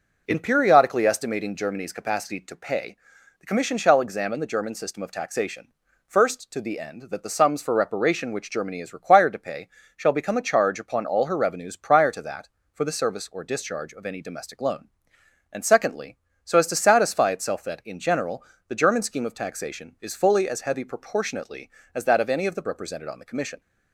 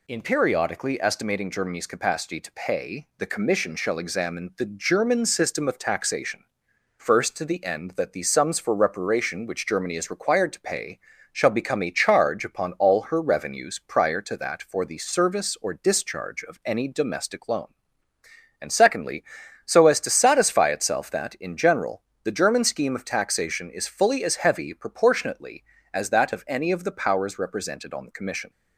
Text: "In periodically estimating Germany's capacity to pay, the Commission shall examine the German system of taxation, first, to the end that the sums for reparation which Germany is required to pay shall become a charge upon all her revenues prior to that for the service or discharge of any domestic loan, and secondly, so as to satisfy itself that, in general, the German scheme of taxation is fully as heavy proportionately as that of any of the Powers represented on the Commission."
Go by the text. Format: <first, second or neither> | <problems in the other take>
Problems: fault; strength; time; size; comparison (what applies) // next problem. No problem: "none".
second | pauses between "pay" and "shall"; slight; at 9.6 s; 0.28 s long; slight in the second // skips "Powers"; at 22.6 s